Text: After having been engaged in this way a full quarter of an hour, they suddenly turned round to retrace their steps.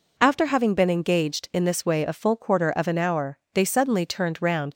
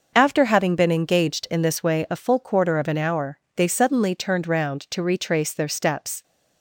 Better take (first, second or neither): second